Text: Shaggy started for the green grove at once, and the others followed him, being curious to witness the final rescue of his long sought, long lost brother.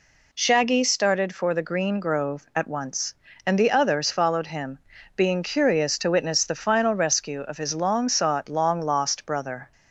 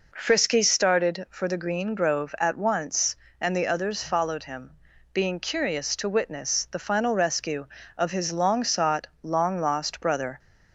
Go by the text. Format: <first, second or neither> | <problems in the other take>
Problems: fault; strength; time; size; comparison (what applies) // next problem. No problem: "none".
first | says "Frisky" for "Shaggy"; at 0.1 s